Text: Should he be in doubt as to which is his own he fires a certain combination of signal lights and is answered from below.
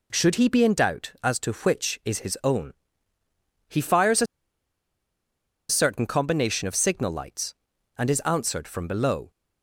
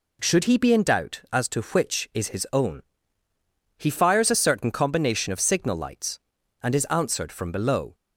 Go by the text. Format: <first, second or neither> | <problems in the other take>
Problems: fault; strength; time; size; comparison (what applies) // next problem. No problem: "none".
second | pauses between "own" and "he"; noticeable; at 2.7 s; 0.96 s long; noticeable in the second // pauses between "a" and "certain"; strong; at 4.2 s; 1.4 s long